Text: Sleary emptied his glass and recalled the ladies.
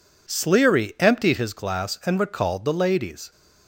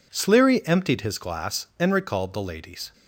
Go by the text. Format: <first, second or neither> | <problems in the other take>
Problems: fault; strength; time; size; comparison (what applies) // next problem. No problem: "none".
neither | none